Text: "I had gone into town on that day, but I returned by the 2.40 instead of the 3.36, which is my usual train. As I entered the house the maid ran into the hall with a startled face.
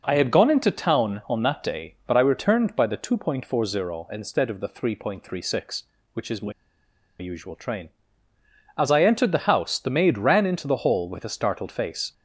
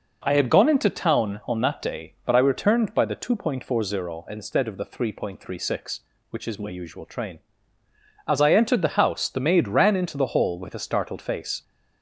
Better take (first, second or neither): second